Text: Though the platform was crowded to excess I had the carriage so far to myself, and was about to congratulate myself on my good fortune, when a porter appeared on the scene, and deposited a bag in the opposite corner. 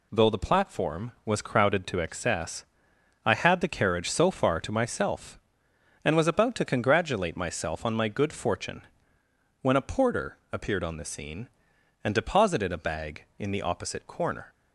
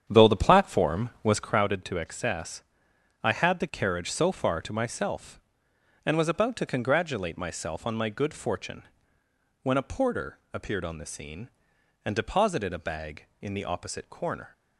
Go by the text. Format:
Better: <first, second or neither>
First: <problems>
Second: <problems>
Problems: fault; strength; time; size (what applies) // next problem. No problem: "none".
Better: first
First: pauses between "excess" and "I"; noticeable; at 2.6 s; 0.60 s long // pauses between "porter" and "appeared"; slight; at 10.3 s; 0.16 s long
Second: starts louder than the rest; strong; until 1.6 s; 8.5 dB // pauses between "excess" and "I"; noticeable; at 2.6 s; 0.60 s long // pauses between "porter" and "appeared"; slight; at 10.3 s; 0.16 s long